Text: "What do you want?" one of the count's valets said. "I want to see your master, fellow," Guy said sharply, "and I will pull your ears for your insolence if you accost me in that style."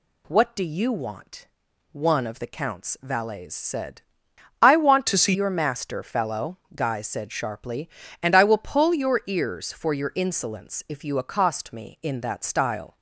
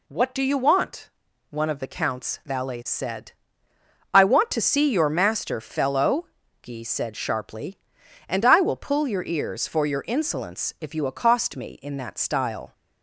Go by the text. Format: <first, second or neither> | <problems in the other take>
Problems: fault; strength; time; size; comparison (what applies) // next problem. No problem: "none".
second | changes voice from "to" to "see"; from 5.0 to 5.3 s; 0.3 s long